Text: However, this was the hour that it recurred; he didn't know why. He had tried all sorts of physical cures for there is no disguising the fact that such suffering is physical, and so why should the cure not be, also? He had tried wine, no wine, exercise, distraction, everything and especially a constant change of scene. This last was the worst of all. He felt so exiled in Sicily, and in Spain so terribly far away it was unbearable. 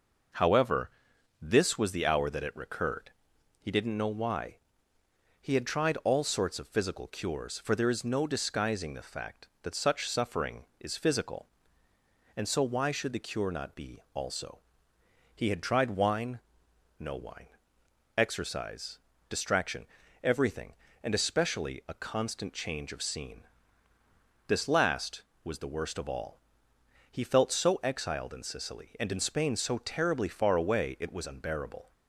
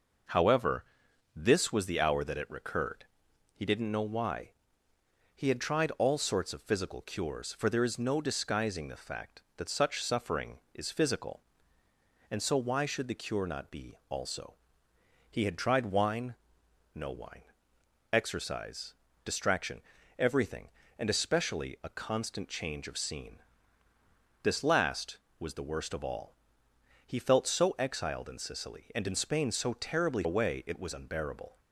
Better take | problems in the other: first | skips "far"; at 30.2 s

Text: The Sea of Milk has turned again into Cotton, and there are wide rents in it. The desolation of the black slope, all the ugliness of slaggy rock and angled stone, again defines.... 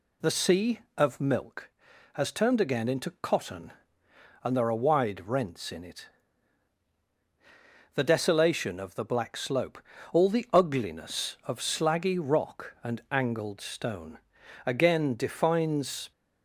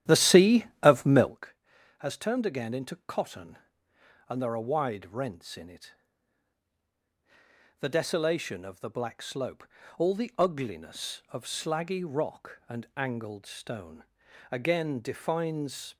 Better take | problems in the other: first | starts louder than the rest; strong; until 1.4 s; 11.5 dB

